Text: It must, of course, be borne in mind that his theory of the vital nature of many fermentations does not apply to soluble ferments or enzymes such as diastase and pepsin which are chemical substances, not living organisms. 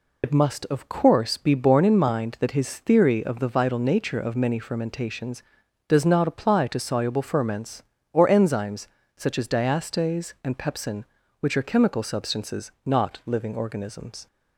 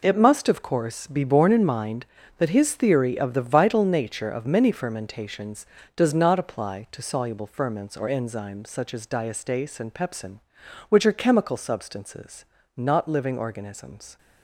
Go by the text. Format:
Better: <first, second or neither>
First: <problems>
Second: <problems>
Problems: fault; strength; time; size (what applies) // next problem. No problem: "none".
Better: second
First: loses the start of "It"; at 0.2 s; 70 ms // pauses between "enzymes" and "such"; slight; at 8.8 s; 0.30 s long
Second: none